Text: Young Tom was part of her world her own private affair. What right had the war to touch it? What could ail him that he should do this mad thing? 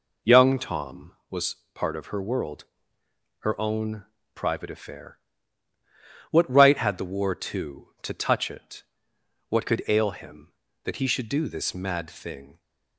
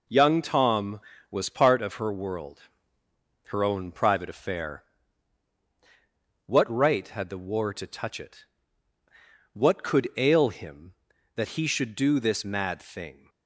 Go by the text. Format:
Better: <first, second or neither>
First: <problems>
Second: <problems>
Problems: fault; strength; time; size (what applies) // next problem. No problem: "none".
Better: second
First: pauses between "was" and "part"; slight; at 1.5 s; 0.18 s long // pauses between "world" and "her"; noticeable; at 2.6 s; 0.74 s long // pauses between "own" and "private"; slight; at 4.0 s; 0.32 s long // says "to" twice; at 8.0 s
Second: pauses between "world" and "her"; noticeable; at 2.6 s; 0.84 s long